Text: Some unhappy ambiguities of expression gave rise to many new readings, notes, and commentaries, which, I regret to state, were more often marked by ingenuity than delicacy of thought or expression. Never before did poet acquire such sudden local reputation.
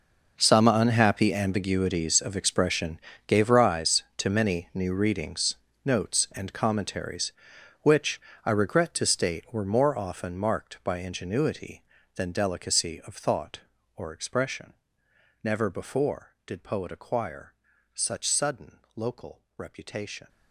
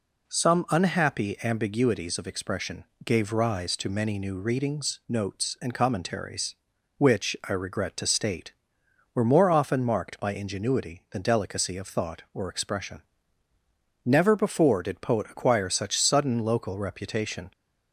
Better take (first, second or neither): second